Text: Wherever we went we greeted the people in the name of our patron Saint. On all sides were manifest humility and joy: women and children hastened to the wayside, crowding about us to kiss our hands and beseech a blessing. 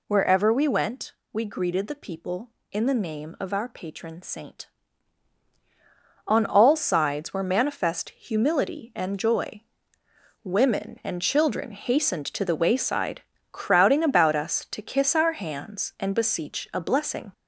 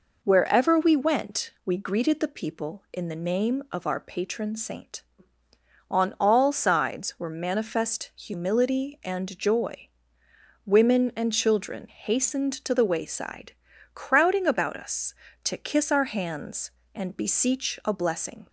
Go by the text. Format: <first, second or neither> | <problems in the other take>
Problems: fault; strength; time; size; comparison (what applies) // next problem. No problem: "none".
second | gets louder; slight; throughout; 3 dB // pauses between "went" and "we"; slight; at 1.1 s; 0.20 s long